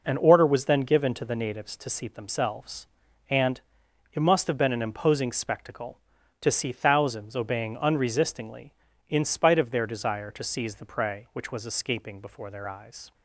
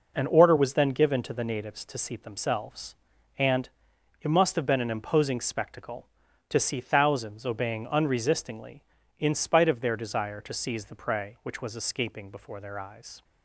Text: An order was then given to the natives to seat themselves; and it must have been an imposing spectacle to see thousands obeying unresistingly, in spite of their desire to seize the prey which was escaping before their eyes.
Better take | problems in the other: neither | pauses between "and" and "it"; noticeable; the same in both

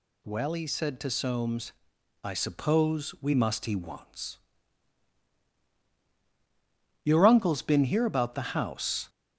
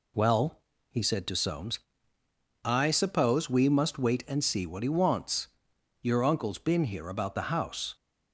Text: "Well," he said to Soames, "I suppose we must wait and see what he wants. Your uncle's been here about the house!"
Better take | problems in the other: second | skips "wait and see what"; at 3.6 s

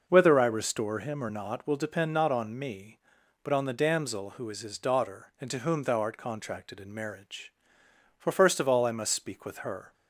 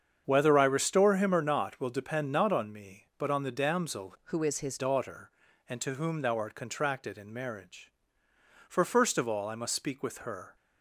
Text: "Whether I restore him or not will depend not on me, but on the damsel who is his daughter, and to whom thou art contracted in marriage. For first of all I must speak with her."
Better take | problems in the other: first | starts louder than the rest; strong; until 1.2 s; 7.5 dB // changes voice from "who" to "his"; from 4.2 to 4.7 s; 0.5 s long

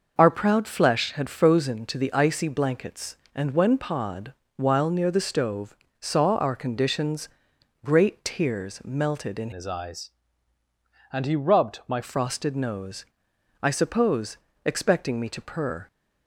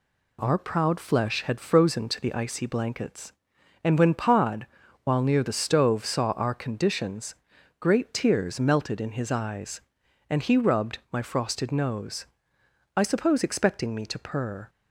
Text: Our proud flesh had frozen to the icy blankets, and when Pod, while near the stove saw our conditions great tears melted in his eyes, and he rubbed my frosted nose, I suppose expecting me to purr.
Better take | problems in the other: second | pauses between "stove" and "saw"; slight; at 5.7 s; 0.24 s long // pauses between "conditions" and "great"; noticeable; at 7.2 s; 0.56 s long; noticeable in the second // changes voice from "his" to "my"; from 9.5 to 12.0 s; 2.5 s long // pauses between "suppose" and "expecting"; slight; at 14.3 s; 0.28 s long

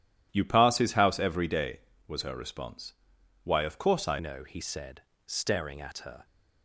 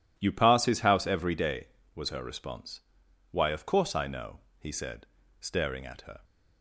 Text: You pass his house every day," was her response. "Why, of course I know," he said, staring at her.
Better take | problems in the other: second | changes voice at "know"; from 4.1 s on; 2.1 s long

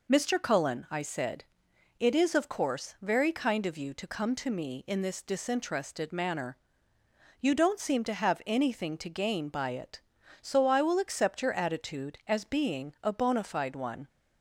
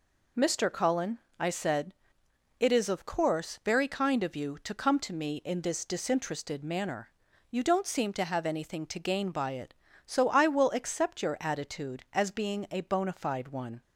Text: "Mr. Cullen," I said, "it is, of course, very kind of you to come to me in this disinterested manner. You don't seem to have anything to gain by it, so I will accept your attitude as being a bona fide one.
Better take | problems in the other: neither | none

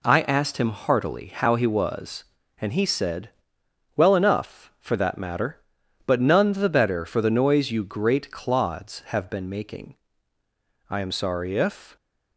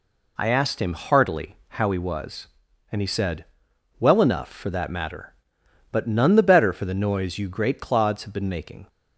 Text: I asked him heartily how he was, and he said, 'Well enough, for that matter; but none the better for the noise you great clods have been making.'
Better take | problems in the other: second | goes on to say "I am sorry if"; noticeable; from 10.8 s on; 1.0 s long

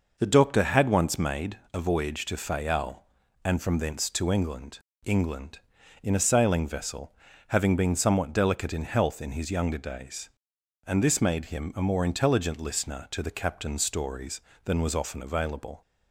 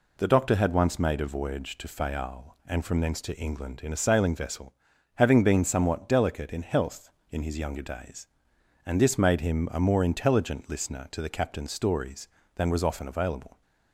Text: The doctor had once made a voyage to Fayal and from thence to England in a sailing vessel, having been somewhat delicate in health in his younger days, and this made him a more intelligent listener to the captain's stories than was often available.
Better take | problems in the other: second | pauses between "made" and "a"; slight; at 1.5 s; 0.16 s long // says "England" twice; at 5.0 s

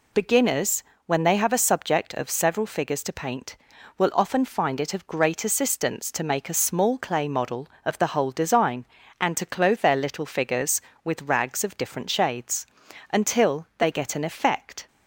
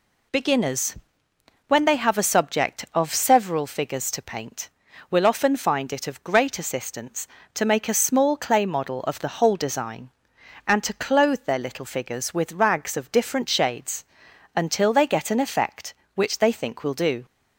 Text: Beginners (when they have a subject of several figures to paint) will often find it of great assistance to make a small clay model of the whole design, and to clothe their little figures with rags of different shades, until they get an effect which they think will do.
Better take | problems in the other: second | stops before "which they think will do"; at 14.8 s

